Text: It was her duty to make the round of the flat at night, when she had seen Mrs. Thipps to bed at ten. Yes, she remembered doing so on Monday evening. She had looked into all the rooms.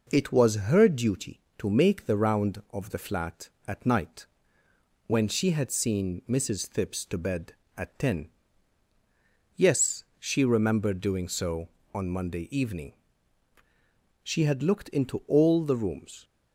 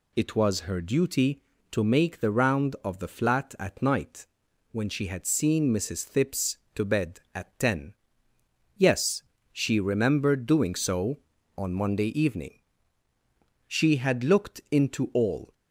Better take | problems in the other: first | stops before "the rooms"; at 15.5 s

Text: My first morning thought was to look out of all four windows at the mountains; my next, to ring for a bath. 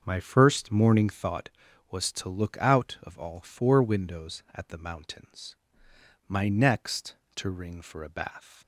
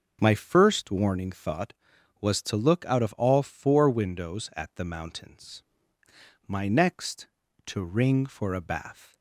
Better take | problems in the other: first | starts louder than the rest; until 1.2 s; 6 dB; also in the first // says "warning" for "morning"; at 0.9 s

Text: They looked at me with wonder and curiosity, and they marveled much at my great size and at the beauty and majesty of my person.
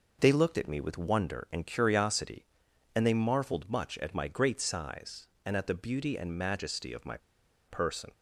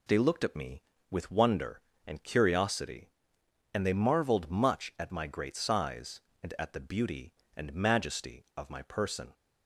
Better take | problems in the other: second | pauses between "my" and "person"; noticeable; at 7.1 s; 0.51 s long

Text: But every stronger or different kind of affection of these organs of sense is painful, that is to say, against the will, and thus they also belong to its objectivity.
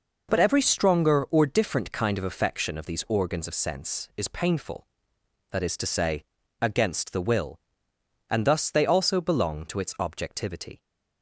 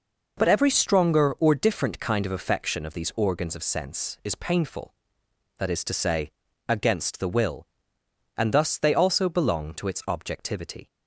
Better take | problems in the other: neither | none

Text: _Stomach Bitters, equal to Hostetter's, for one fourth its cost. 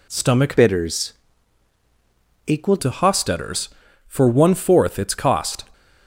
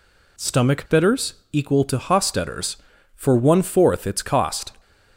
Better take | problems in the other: second | changes voice from "Bitters" to "equal"; from 0.5 to 2.7 s; 2.2 s long

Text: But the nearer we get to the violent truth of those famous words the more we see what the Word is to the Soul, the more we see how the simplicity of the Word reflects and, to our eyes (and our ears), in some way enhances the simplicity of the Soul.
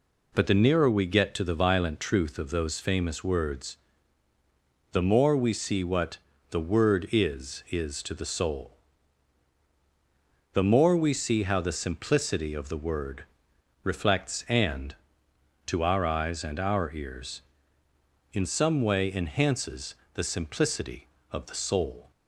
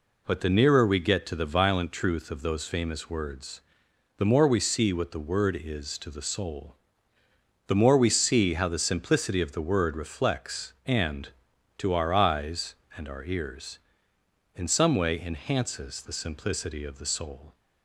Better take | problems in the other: second | pauses between "words" and "the"; at 3.7 s; 1.1 s long; noticeable in the second // pauses between "what" and "the"; slight; at 6.1 s; 0.32 s long // says "is" twice; at 7.7 s // pauses between "Word" and "reflects"; noticeable; at 13.2 s; 0.60 s long // pauses between "enhances" and "the"; slight; at 19.9 s; 0.18 s long

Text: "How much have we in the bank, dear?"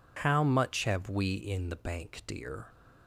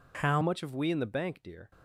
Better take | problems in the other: first | changes voice at "much"; from 0.4 s on; 1.3 s long

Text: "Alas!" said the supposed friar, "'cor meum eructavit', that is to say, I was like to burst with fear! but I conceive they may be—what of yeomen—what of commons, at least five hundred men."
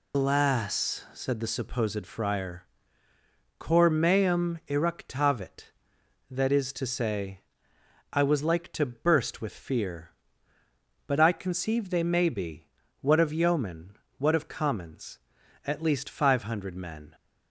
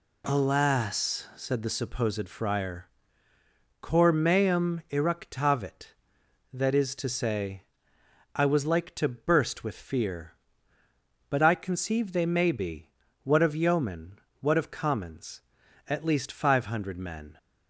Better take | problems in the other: second | loses the start of "Alas"; at 0.1 s; 130 ms

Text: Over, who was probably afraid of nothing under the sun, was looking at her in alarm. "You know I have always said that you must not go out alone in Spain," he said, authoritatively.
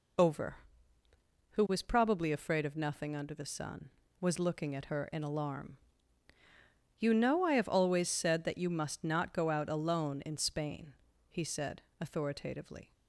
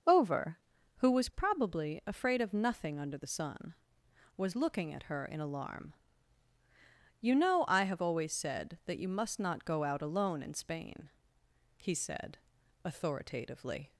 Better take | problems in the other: neither | none

